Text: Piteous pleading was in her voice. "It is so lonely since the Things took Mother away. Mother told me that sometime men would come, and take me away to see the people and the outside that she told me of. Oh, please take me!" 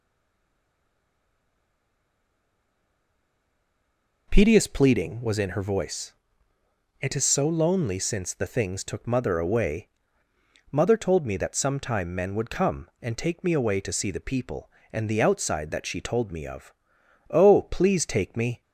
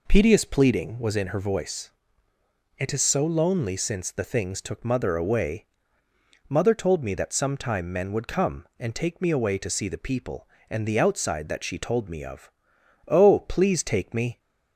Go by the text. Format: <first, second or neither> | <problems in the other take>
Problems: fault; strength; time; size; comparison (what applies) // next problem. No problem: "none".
second | stays silent before the first word; strong; until 4.2 s; 4.2 s long